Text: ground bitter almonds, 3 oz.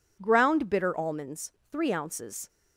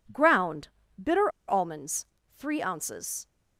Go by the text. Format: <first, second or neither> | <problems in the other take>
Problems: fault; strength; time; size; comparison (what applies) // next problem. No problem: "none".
first | pauses between "ground" and "bitter"; slight; at 0.6 s; 0.28 s long // pauses between "bitter" and "almonds"; slight; at 1.2 s; 0.19 s long